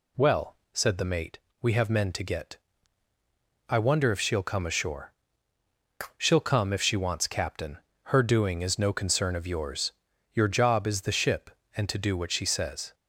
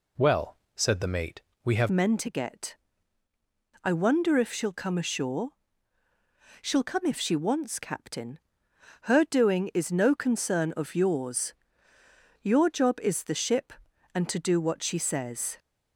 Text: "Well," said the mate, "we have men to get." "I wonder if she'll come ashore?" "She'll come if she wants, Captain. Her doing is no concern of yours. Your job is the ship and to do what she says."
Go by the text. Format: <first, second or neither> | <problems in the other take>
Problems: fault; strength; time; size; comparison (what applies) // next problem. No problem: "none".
first | changes voice at "men"; from 1.9 s on; 13.6 s long